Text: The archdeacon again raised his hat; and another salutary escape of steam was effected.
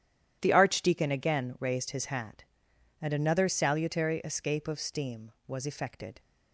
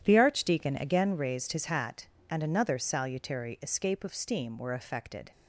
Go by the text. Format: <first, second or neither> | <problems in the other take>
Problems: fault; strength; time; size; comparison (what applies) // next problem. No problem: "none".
first | starts louder than the rest; strong; until 1.0 s; 10.5 dB // says "were" for "was"; at 4.5 s